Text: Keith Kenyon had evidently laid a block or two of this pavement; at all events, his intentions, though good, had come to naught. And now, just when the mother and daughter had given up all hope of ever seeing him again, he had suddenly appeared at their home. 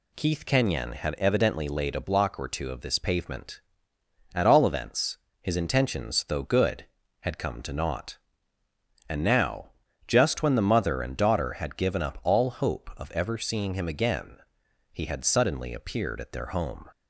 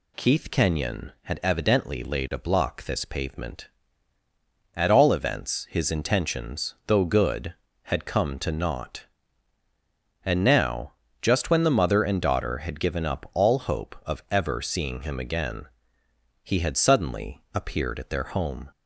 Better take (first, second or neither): first